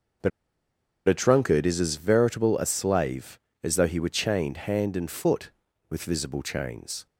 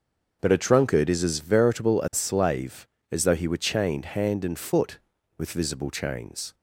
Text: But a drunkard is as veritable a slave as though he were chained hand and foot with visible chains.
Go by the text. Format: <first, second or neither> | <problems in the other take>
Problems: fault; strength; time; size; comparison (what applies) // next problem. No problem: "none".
second | starts louder than the rest; until 1.9 s; 6.5 dB; also in the second // pauses between "But" and "a"; noticeable; at 0.3 s; 0.77 s long